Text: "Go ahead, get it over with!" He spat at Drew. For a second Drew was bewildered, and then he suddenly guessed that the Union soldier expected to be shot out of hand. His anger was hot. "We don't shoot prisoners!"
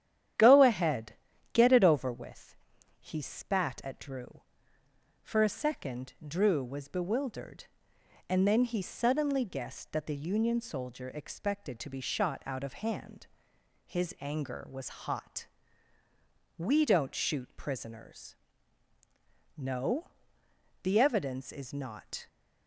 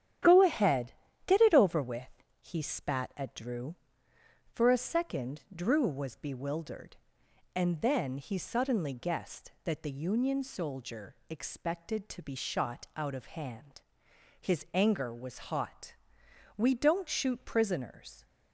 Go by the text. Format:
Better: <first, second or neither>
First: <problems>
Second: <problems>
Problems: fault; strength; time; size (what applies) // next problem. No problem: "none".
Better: second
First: starts louder than the rest; strong; until 1.7 s; 10.5 dB // goes on to say "No The evidence is not"; strong; from 19.5 s on; 2.7 s long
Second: starts louder than the rest; strong; until 1.5 s; 10.5 dB